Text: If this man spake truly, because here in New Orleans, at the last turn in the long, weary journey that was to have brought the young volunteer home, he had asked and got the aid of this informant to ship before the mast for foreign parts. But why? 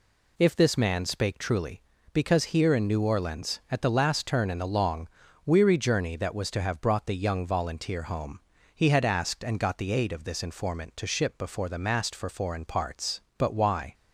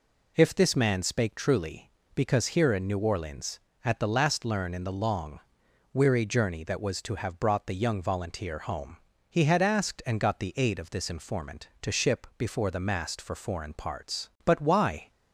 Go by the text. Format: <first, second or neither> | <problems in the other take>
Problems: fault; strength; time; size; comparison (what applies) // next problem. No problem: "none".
first | says "learn" for "turn"; at 4.4 s